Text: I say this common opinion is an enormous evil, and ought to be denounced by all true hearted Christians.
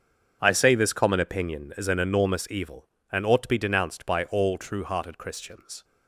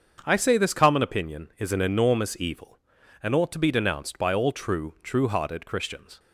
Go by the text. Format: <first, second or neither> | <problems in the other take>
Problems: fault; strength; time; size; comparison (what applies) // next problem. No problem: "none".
first | starts louder than the rest; until 1.2 s; 7 dB; also in the first // says "true" twice; at 5.0 s